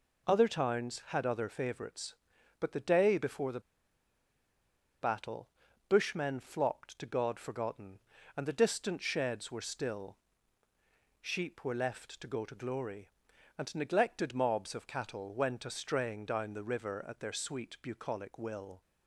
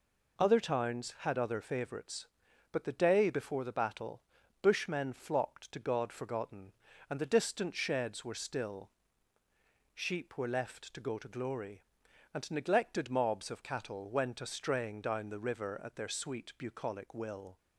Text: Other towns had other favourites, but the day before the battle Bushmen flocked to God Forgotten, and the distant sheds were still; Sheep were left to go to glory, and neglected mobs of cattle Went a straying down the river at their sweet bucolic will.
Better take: second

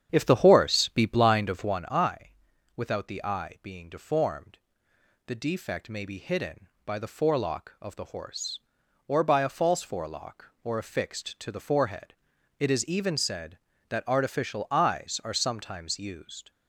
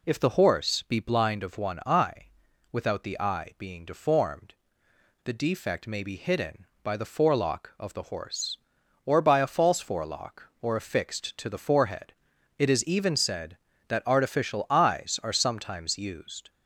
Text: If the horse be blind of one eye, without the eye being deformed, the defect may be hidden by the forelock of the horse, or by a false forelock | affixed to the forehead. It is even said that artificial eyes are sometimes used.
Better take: second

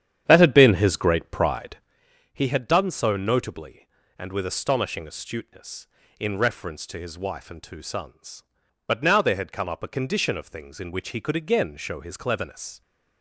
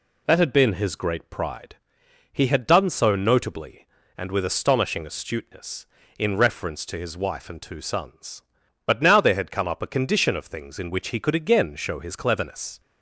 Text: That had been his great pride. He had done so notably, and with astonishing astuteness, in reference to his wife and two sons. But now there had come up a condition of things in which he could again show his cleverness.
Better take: second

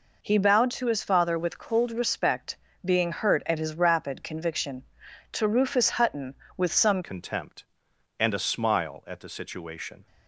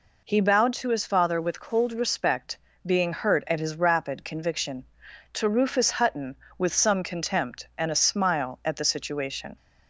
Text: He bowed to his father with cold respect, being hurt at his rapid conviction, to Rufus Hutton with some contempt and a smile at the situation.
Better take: second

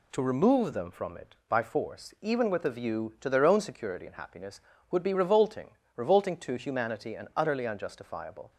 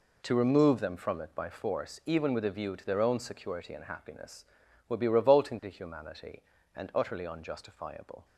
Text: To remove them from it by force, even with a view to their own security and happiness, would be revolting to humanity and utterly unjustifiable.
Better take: second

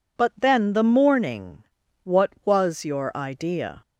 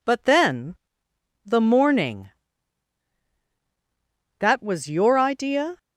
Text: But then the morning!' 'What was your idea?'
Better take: first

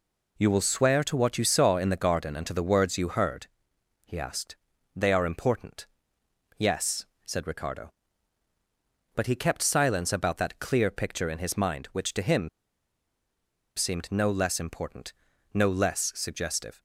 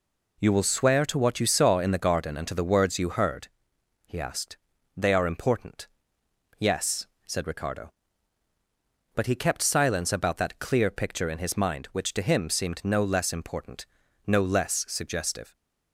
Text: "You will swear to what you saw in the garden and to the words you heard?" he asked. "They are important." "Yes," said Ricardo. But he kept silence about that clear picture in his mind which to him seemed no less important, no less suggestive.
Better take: second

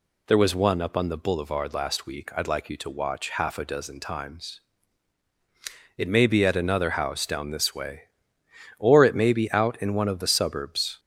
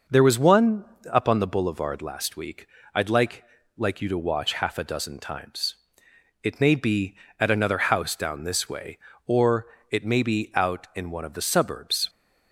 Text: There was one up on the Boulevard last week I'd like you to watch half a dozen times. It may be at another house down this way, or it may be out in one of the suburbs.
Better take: first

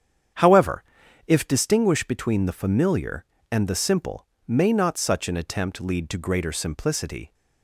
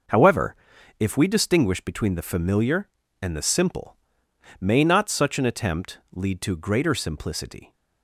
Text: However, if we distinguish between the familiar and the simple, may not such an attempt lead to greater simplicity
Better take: second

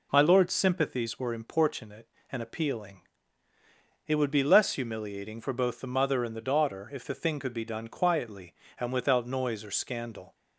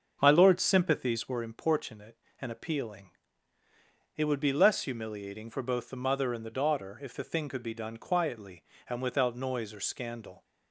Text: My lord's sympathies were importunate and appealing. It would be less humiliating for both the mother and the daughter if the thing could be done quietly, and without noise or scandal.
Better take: first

